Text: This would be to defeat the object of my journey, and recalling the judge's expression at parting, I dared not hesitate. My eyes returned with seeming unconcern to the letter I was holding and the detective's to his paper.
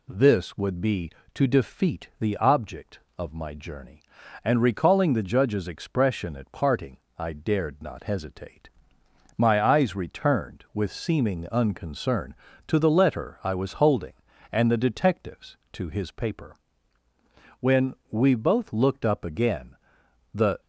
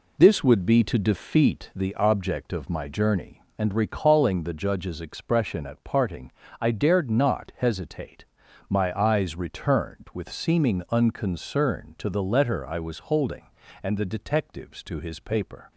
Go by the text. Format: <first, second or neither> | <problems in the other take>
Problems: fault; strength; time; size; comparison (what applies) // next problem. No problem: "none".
second | goes on to say "When we both looked up again the"; strong; from 17.5 s on; 3.0 s long